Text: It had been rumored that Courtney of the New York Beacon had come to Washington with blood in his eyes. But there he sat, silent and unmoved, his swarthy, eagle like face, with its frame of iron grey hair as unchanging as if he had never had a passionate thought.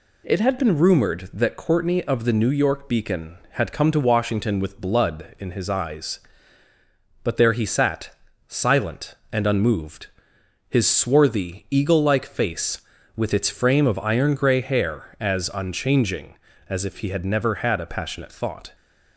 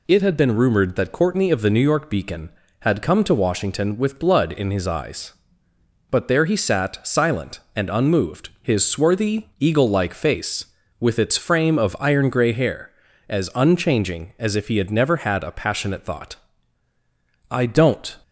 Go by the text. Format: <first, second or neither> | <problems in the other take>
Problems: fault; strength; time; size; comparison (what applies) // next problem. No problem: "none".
first | goes on to say "I don't"; noticeable; from 17.4 s on; 0.68 s long